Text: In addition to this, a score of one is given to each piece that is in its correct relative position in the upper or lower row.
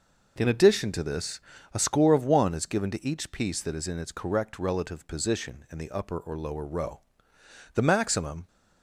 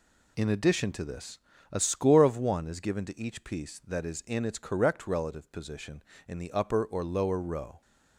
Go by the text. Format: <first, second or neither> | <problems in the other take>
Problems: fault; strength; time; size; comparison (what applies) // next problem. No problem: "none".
second | goes on to say "The maximum"; noticeable; from 7.7 s on; 0.72 s long